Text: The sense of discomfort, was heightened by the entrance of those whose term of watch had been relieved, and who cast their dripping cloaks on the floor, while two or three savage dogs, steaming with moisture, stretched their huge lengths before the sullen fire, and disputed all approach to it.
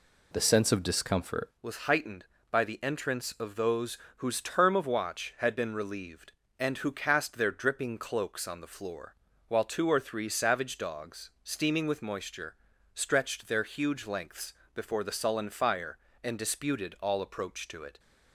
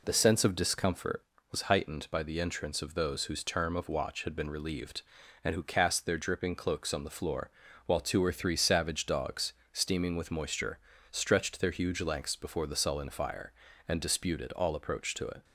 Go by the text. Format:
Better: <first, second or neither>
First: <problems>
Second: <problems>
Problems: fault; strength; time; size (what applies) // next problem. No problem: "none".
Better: second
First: changes voice at "was"; from 1.6 s on; 16.3 s long // pauses between "those" and "whose"; slight; at 3.9 s; 0.20 s long // pauses between "lengths" and "before"; slight; at 14.5 s; 0.22 s long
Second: none